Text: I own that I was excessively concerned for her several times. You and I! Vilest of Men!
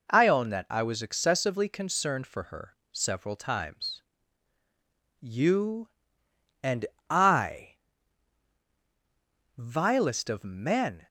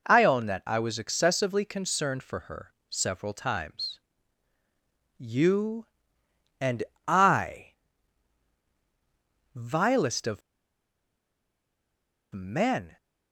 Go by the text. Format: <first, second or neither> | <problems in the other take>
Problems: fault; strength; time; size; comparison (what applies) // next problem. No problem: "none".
first | pauses between "her" and "several"; slight; at 2.7 s; 0.16 s long; slight in the first // pauses between "and" and "I"; slight; at 6.8 s; 0.24 s long; slight in the first // pauses between "of" and "Men"; strong; at 10.4 s; 1.9 s long